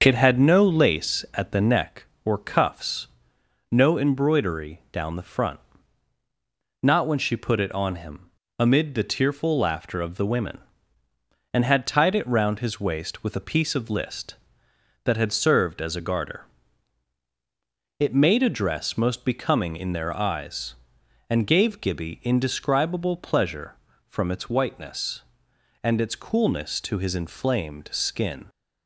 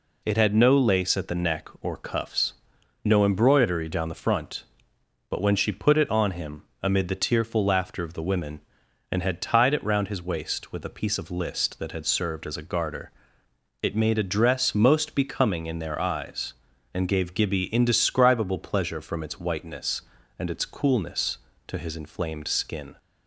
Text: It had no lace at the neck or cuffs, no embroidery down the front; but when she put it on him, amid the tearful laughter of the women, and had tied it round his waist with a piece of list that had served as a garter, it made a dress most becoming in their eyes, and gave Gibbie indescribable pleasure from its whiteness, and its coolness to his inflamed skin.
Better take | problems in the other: second | starts louder than the rest; until 1.0 s; 6.5 dB // says "not" for "but"; at 6.8 s

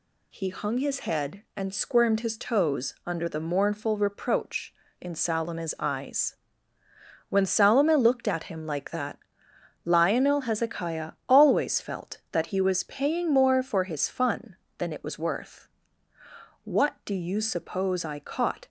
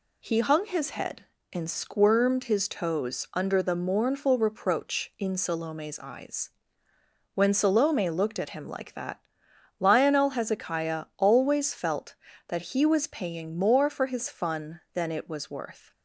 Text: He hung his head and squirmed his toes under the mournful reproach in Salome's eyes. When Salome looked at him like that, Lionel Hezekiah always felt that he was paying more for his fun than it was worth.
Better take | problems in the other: second | pauses between "Hezekiah" and "always"; slight; at 11.1 s; 0.16 s long // goes on to say "What do you suppose I caught"; strong; from 16.6 s on; 2.0 s long

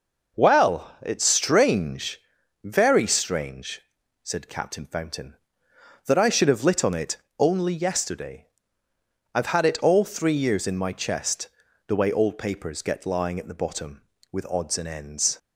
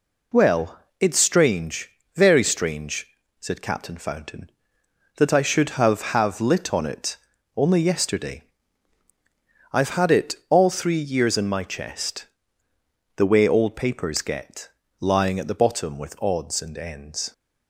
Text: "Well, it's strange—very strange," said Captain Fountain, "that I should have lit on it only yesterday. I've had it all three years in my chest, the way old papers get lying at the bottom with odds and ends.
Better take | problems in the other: first | says "have" twice; at 6.1 s // pauses between "it" and "only"; slight; at 7.1 s; 0.36 s long; slight in the first // pauses between "get" and "lying"; slight; at 14.7 s; 0.30 s long

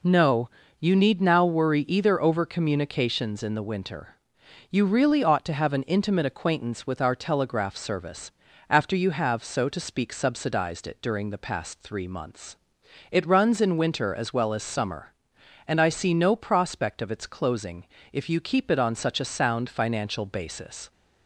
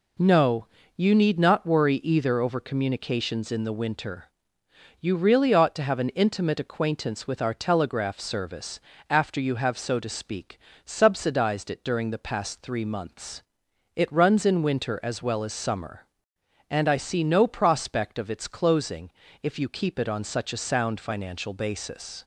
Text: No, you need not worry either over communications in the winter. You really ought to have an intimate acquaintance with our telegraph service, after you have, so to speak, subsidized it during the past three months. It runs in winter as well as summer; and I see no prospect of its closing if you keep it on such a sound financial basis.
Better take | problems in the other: second | says "now" for "not"; at 1.2 s // pauses between "closing" and "if"; slight; at 17.8 s; 0.28 s long; slight in the second

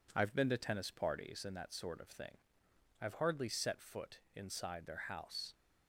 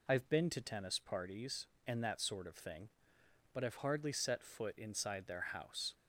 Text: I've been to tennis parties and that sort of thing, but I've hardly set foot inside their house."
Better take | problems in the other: second | skips "but"; at 2.6 s // pauses between "foot" and "inside"; slight; at 4.1 s; 0.16 s long

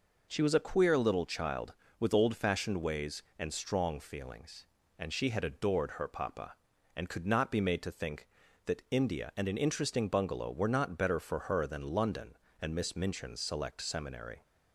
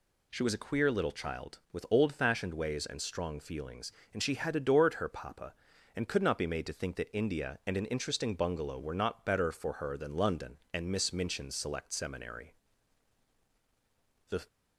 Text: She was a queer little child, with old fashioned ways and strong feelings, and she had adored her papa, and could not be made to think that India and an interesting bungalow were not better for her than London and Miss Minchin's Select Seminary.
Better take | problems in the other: first | goes on to say "The"; slight; from 14.2 s on; 0.18 s long

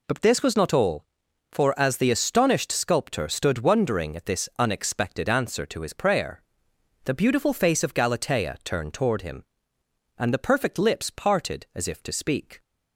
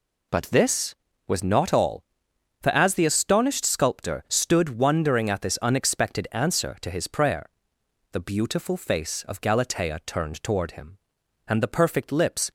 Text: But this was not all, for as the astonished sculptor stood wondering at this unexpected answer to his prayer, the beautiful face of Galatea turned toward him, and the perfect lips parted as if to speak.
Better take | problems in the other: first | stops before "parted as if to speak"; at 12.4 s

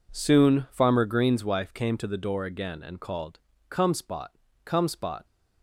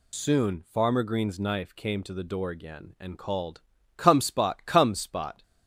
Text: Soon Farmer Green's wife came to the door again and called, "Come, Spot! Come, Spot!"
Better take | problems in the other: first | says "knife" for "wife"; at 1.3 s

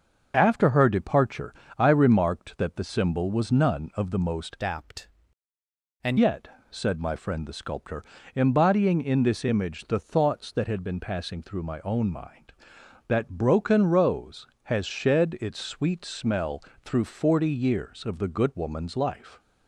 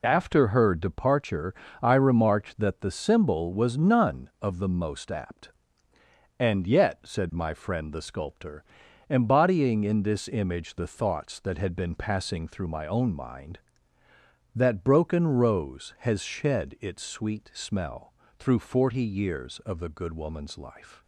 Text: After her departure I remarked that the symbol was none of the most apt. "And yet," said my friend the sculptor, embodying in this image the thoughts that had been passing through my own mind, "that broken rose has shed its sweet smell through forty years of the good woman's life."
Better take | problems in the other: second | starts louder than the rest; until 1.3 s; 6 dB // pauses between "departure" and "I"; slight; at 1.5 s; 0.24 s long; slight in the second // changes voice from "apt" to "And"; from 4.6 to 6.1 s; 1.5 s long // pauses between "smell" and "through"; slight; at 16.6 s; 0.22 s long; slight in the second

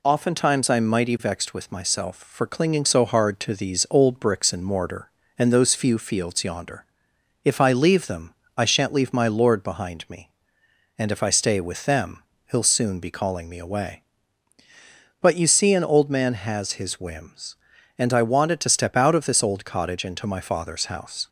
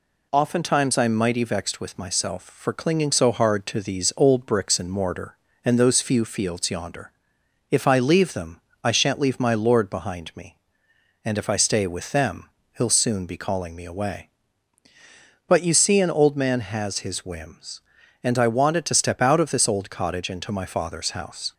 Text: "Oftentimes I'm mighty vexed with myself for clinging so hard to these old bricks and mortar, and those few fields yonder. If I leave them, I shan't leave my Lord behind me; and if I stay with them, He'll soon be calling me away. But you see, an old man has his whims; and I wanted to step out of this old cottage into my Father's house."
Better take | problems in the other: neither | none

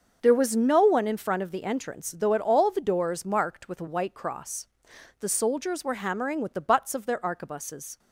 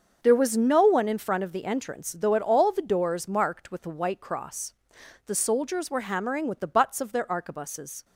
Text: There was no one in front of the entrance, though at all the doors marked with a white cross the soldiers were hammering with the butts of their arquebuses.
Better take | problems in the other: neither | starts louder than the rest; the same in both // pauses between "cross" and "the"; noticeable; the same in both

